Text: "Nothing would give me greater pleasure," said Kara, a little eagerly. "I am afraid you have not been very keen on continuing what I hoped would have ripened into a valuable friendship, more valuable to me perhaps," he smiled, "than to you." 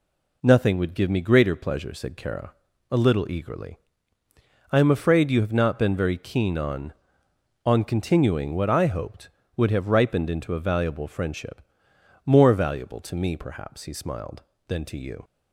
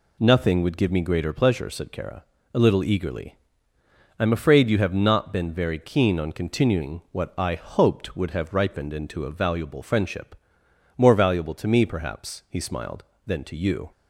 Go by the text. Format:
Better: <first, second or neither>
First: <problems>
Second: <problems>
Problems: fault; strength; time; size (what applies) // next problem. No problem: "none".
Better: second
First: says "on" twice; at 7.6 s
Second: none